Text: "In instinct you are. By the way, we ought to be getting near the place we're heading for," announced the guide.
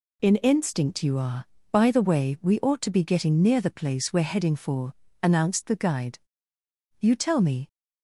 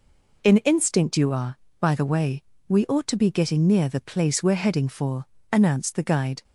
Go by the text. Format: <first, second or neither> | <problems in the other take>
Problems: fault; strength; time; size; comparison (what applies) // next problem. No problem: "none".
second | goes on to say "You tell me"; noticeable; from 7.0 s on; 0.66 s long